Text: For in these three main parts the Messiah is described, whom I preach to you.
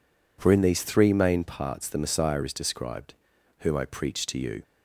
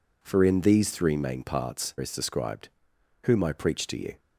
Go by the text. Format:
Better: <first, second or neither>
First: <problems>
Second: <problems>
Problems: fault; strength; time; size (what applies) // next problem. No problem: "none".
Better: first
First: none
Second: skips "the Messiah"; at 1.9 s